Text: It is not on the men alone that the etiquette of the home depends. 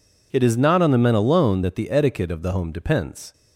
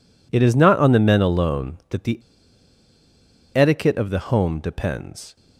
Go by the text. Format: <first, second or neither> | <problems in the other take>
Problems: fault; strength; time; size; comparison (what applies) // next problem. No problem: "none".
first | pauses between "the" and "etiquette"; strong; at 2.1 s; 1.3 s long